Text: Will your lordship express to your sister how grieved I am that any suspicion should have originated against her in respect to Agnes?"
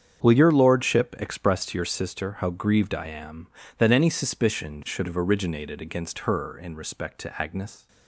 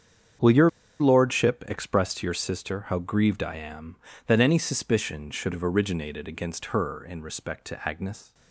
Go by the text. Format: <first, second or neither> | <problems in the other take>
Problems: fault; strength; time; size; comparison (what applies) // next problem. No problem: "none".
first | starts louder than the rest; strong; until 1.7 s; 7.5 dB; strong in the first // pauses between "your" and "lordship"; slight; at 0.6 s; 0.30 s long